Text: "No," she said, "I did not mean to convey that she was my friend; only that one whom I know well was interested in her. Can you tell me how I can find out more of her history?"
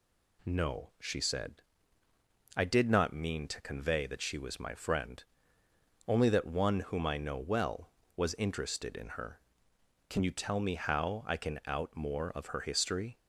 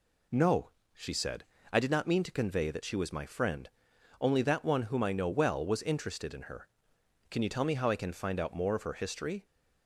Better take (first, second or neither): second